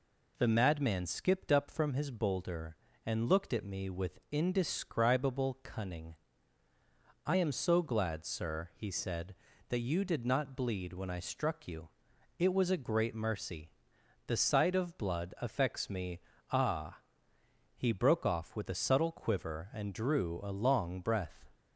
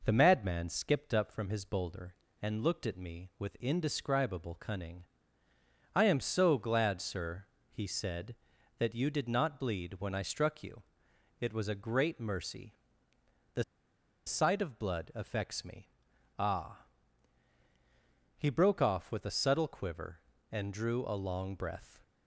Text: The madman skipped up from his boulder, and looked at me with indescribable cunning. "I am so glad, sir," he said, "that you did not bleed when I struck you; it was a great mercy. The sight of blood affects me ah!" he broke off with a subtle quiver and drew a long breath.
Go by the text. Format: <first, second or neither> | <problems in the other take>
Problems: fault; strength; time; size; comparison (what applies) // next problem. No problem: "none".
first | pauses between "The" and "sight"; noticeable; at 13.6 s; 0.62 s long // pauses between "me" and "ah"; noticeable; at 15.9 s; 0.48 s long; slight in the first